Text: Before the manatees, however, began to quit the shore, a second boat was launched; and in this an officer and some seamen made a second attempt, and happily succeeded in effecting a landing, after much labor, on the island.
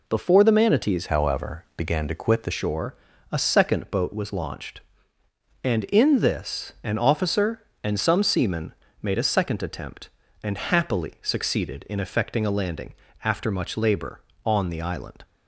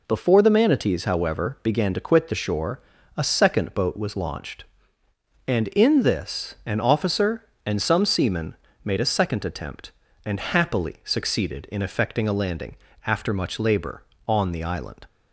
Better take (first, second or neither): second